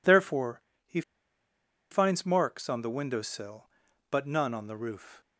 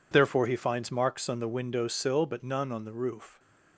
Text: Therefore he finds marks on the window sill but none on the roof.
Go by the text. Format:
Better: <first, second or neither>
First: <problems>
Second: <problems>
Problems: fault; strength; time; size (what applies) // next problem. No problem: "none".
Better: second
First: pauses between "Therefore" and "he"; slight; at 0.6 s; 0.24 s long // pauses between "he" and "finds"; noticeable; at 1.0 s; 0.90 s long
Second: none